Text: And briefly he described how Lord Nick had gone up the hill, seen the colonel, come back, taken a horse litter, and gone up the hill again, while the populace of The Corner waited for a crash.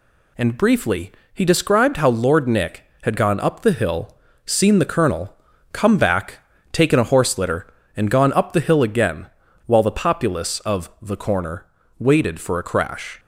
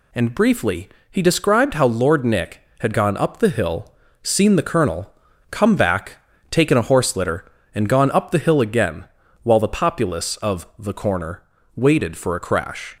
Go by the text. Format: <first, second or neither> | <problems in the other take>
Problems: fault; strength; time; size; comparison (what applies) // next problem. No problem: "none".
neither | pauses between "briefly" and "he"; slight; the same in both // pauses between "Corner" and "waited"; slight; the same in both